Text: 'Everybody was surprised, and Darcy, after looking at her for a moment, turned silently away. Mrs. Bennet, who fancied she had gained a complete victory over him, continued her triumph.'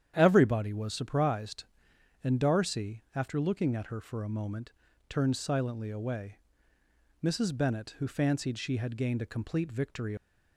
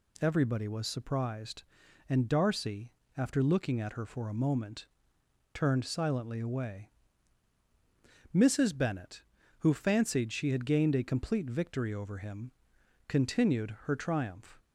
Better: second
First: starts louder than the rest; strong; until 1.1 s; 9.5 dB // stops before "over him continued her triumph"; at 10.1 s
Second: none

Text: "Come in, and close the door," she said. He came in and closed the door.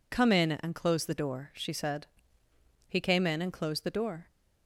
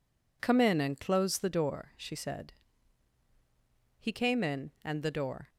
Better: first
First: none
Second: skips "closed"; at 5.0 s

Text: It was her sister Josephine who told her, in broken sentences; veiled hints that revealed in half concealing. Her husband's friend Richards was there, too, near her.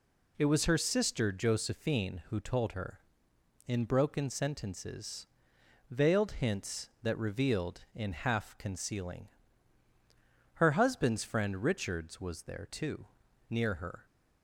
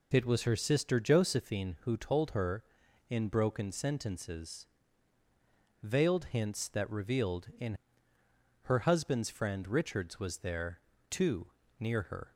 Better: first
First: none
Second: skips "half concealing"; at 8.1 s

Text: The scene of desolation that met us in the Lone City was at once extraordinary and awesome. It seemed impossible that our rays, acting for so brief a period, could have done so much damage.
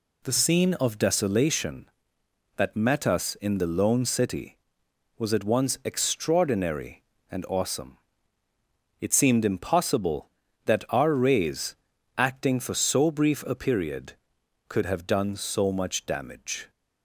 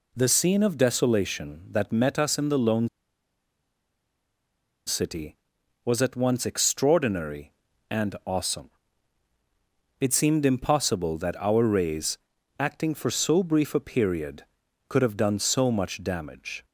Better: first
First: none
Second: pauses between "Lone" and "City"; strong; at 2.8 s; 1.9 s long

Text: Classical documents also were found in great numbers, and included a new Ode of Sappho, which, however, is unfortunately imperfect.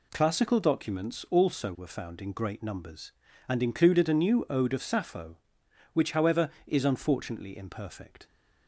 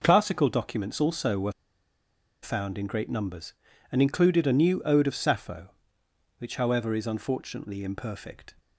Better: first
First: none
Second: pauses between "were" and "found"; noticeable; at 1.5 s; 0.90 s long

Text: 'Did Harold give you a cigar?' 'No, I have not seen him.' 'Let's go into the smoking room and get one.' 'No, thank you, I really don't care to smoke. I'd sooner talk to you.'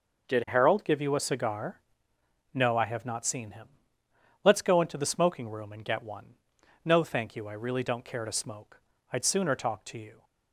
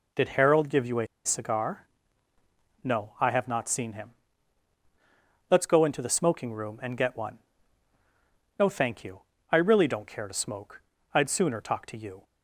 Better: first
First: none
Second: pauses between "a" and "cigar"; slight; at 1.0 s; 0.18 s long

